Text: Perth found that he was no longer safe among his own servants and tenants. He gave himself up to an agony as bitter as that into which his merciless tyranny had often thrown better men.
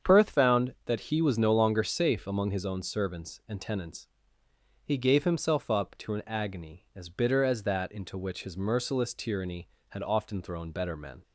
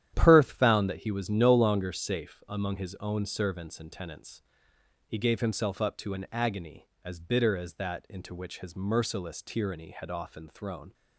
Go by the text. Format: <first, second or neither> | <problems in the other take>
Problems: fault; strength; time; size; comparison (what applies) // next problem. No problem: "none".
first | starts louder than the rest; strong; until 1.1 s; 10.5 dB; strong in the first // stops before "better men"; at 10.9 s